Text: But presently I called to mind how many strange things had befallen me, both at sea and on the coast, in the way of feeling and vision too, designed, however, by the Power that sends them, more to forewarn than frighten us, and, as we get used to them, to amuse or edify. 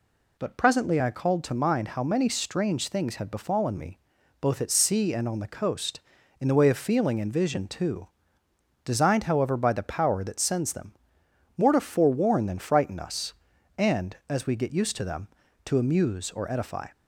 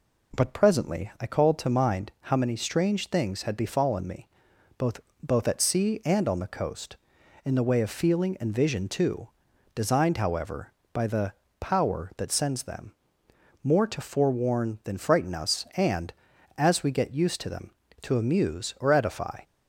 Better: first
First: none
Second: says "both" twice; at 5.2 s // pauses between "the" and "Power"; slight; at 11.3 s; 0.28 s long

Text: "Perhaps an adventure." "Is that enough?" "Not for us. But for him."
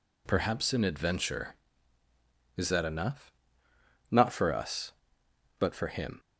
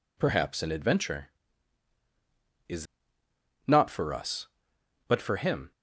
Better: first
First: none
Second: skips "that enough"; at 3.2 s

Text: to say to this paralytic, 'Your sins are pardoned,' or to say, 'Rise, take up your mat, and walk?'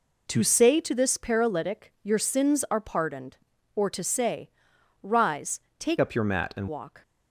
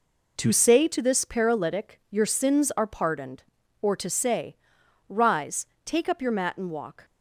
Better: second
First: changes voice from "up" to "and"; from 6.0 to 6.6 s; 0.6 s long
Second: none

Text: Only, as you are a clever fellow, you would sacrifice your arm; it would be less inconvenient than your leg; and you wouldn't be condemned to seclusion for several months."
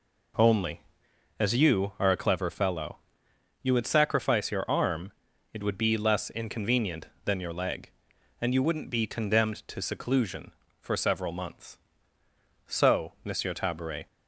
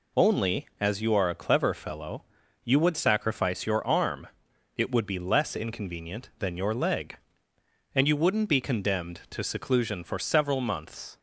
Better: second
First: goes on to say "So Monsieur Tabaret"; from 12.6 s on; 1.4 s long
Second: none

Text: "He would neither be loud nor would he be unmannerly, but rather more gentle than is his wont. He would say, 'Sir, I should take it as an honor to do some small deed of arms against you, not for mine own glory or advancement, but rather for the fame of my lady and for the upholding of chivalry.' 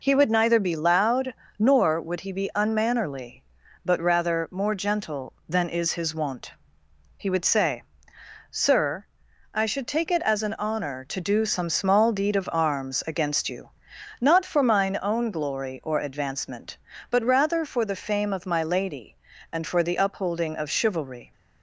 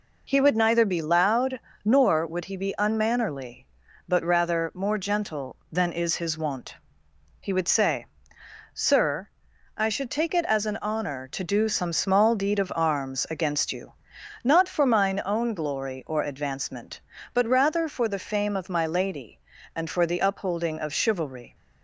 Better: neither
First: pauses between "loud" and "nor"; slight; at 1.3 s; 0.28 s long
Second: pauses between "loud" and "nor"; slight; at 1.5 s; 0.28 s long

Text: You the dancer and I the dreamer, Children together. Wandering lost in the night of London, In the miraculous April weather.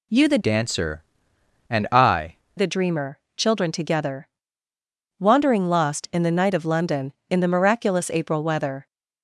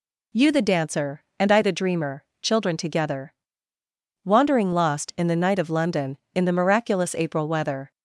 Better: second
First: changes voice from "dancer" to "I"; from 0.4 to 2.3 s; 1.9 s long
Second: none

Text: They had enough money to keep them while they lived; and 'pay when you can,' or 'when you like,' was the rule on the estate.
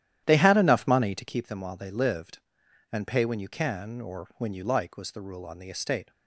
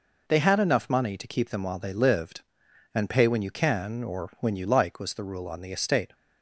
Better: second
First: starts louder than the rest; strong; until 1.4 s; 11.5 dB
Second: none

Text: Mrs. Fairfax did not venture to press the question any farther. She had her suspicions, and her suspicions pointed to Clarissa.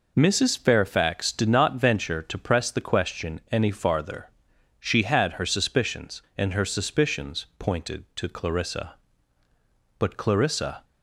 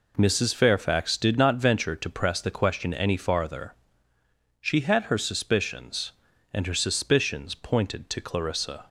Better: second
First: goes on to say "But Clarissa"; noticeable; from 9.9 s on; 0.86 s long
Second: none

